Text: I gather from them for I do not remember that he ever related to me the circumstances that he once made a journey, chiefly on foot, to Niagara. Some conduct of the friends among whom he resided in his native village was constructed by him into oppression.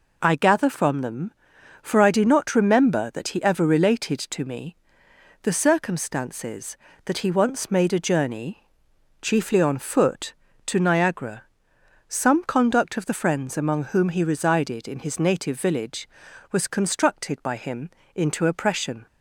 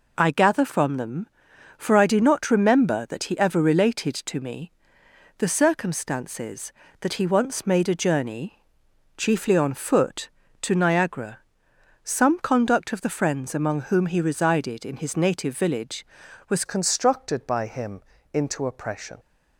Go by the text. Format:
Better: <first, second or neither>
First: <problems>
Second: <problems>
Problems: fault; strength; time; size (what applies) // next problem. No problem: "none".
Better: first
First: pauses between "me" and "the"; noticeable; at 4.7 s; 0.68 s long // pauses between "him" and "into"; slight; at 17.9 s; 0.26 s long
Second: pauses between "me" and "the"; noticeable; at 4.7 s; 0.68 s long // changes voice at "constructed"; from 16.6 s on; 2.5 s long // pauses between "him" and "into"; slight; at 18.0 s; 0.32 s long